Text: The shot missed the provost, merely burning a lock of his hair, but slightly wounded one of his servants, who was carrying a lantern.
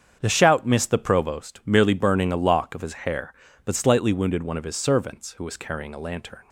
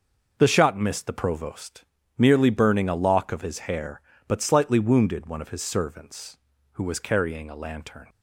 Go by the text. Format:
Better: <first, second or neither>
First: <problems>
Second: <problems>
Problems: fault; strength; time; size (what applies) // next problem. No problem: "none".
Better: second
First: starts louder than the rest; strong; until 1.2 s; 8 dB // says "shout" for "shot"; at 0.2 s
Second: none